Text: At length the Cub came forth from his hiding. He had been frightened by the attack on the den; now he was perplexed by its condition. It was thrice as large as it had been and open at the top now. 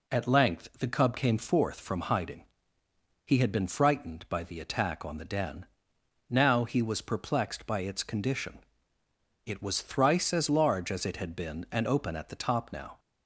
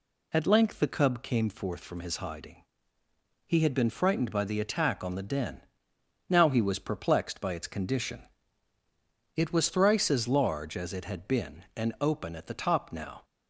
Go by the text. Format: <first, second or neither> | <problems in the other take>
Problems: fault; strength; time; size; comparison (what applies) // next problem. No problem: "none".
second | skips "his"; at 2.0 s